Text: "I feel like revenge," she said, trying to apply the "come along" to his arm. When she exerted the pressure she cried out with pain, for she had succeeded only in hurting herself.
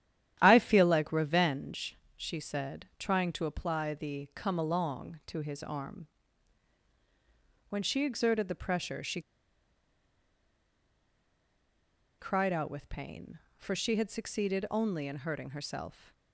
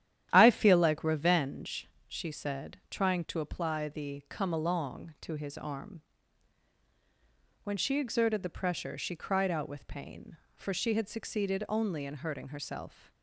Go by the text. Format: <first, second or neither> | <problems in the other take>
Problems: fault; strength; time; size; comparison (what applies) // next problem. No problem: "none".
second | starts louder than the rest; strong; until 1.4 s; 11 dB; strong in the second // pauses between "she" and "cried"; strong; at 9.2 s; 2.9 s long